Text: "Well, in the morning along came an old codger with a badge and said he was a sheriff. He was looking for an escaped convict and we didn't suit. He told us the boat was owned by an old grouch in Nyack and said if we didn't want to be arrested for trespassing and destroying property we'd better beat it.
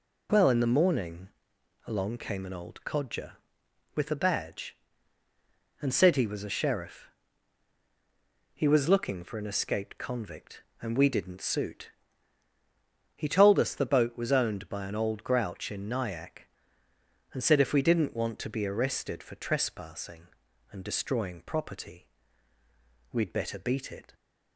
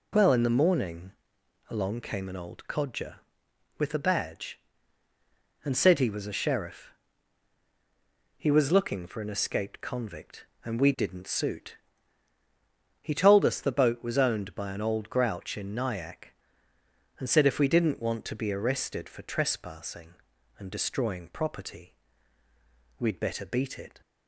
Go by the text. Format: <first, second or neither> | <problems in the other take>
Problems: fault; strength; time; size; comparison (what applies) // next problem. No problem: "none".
neither | pauses between "morning" and "along"; noticeable; the same in both // pauses between "property" and "we'd"; the same in both